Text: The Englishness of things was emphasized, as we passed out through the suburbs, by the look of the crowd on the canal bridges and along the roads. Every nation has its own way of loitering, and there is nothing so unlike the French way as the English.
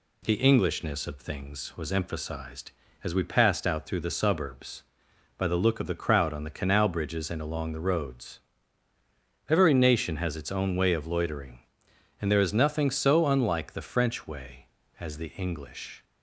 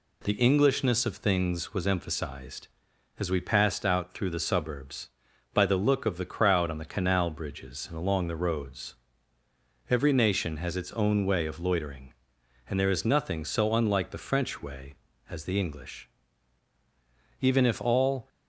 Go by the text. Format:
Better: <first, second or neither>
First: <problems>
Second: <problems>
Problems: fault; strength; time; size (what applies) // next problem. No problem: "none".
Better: first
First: none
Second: goes on to say "Even if all"; noticeable; from 17.4 s on; 0.88 s long